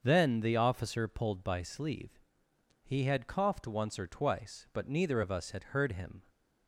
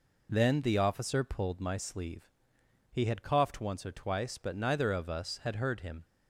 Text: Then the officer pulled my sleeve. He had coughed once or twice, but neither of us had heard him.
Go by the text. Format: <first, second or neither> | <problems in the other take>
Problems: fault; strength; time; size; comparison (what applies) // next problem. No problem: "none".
second | starts louder than the rest; until 1.0 s; 6.5 dB // says "by" for "my"; at 1.4 s